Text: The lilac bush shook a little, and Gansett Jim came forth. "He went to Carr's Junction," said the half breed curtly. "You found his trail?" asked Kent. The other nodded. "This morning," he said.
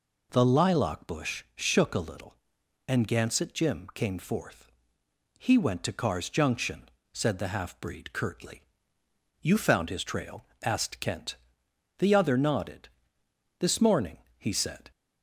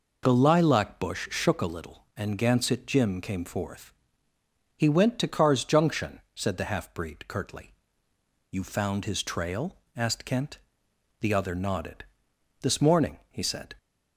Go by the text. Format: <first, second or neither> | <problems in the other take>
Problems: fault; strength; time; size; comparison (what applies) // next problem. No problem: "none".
neither | none